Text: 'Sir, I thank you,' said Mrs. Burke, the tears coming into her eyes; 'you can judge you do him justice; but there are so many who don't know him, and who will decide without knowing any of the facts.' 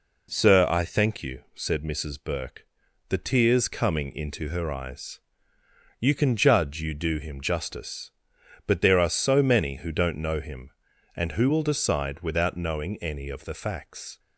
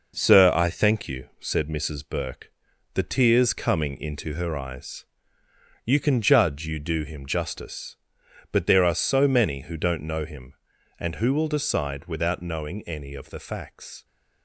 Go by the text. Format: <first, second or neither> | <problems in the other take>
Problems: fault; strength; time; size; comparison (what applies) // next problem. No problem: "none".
first | gets quieter; noticeable; throughout; 6 dB